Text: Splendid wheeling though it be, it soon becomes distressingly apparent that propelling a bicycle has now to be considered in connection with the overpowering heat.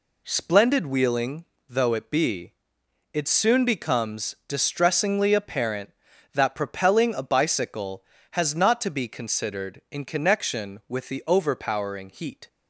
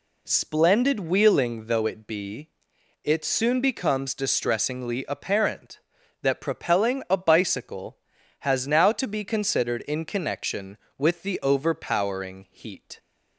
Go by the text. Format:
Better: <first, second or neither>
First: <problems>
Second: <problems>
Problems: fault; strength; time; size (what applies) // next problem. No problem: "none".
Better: second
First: pauses between "wheeling" and "though"; slight; at 1.4 s; 0.22 s long // says "not" for "now"; at 8.5 s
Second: none